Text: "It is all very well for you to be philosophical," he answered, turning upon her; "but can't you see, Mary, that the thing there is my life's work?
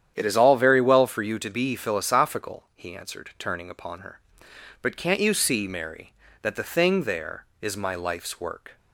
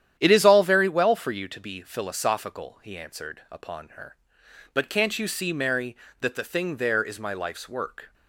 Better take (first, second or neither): first